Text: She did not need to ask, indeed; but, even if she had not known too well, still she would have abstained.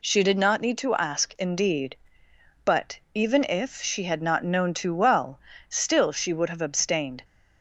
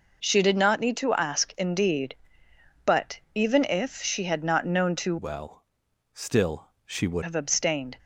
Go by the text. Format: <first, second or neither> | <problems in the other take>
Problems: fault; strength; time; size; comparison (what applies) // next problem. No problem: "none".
first | changes voice from "well" to "would"; from 5.1 to 7.2 s; 2.1 s long // pauses between "still" and "she"; slight; at 6.6 s; 0.16 s long